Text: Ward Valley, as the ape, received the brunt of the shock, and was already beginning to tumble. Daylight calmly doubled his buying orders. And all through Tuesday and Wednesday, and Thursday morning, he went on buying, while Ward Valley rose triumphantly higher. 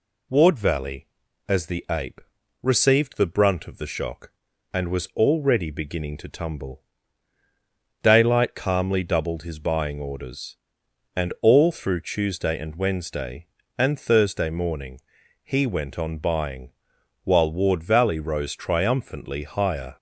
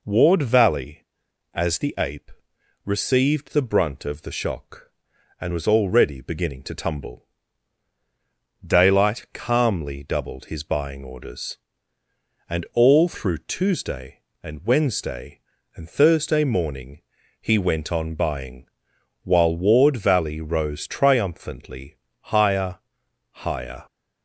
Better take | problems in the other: first | pauses between "triumphantly" and "higher"; slight; at 21.9 s; 0.22 s long // says "higher" twice; at 23.3 s

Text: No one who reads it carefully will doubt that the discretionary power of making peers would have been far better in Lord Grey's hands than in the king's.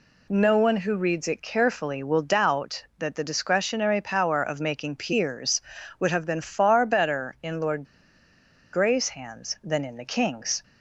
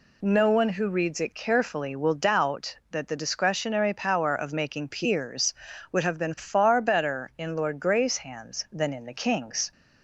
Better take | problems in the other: second | pauses between "Lord" and "Grey's"; noticeable; at 7.8 s; 0.89 s long

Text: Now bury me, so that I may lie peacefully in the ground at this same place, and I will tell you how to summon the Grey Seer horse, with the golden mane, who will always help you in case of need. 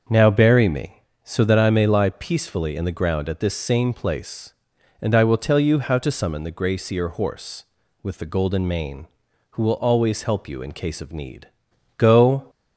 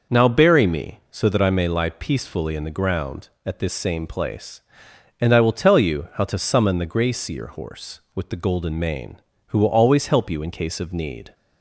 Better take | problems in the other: second | starts louder than the rest; until 1.3 s; 6.5 dB // goes on to say "Go"; from 11.9 s on; 0.52 s long

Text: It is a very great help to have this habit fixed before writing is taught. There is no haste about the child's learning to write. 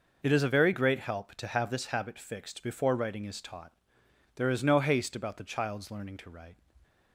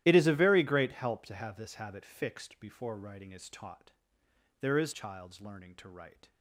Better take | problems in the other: first | starts louder than the rest; strong; until 1.0 s; 13 dB // skips "no haste about the"; at 4.9 s

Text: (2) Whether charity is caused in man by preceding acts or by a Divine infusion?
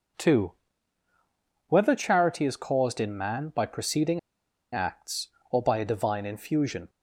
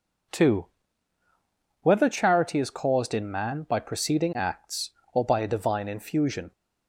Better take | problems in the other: second | pauses between "preceding" and "acts"; noticeable; at 4.1 s; 0.53 s long

